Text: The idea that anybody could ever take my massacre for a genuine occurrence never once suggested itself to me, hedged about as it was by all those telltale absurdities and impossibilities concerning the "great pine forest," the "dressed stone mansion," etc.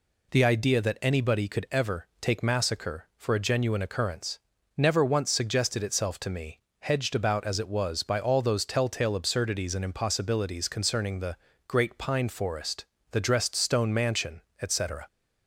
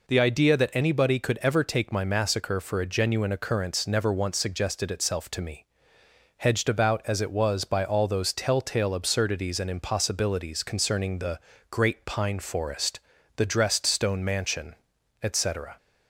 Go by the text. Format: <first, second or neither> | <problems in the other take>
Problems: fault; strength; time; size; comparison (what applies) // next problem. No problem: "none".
second | skips "my"; at 2.4 s // pauses between "occurrence" and "never"; at 4.3 s; 0.38 s long // pauses between "the" and "great"; slight; at 11.3 s; 0.32 s long; slight in the second